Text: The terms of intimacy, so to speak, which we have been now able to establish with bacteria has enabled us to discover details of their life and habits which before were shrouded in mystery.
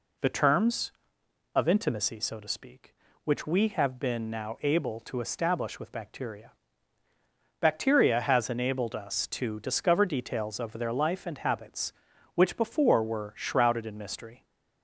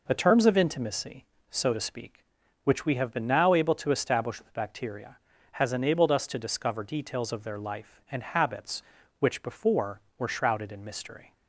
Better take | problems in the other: second | says "bacteria" twice; at 7.5 s

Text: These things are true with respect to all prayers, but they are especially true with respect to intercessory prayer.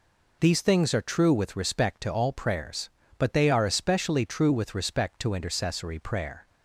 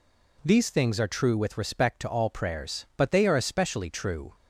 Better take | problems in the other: first | stops before "with respect to intercessory prayer"; at 4.3 s

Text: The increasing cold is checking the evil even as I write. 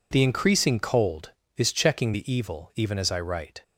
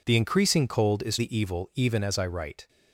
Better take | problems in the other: first | skips "checking"; at 1.1 s

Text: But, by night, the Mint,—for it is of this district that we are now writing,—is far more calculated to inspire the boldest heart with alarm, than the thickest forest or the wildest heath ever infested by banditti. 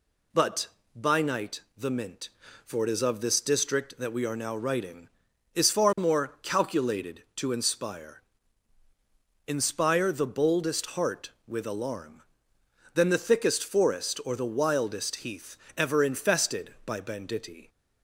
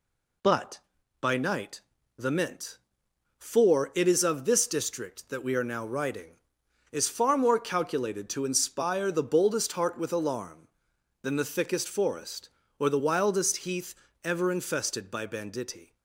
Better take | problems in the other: second | says "inspire" twice; at 9.4 s // pauses between "heath" and "ever"; slight; at 15.5 s; 0.22 s long; slight in the second

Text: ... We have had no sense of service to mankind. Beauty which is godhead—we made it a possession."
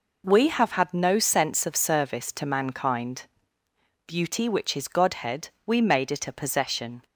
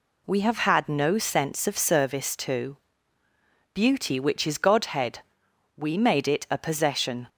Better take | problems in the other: first | skips "mankind"; at 3.2 s

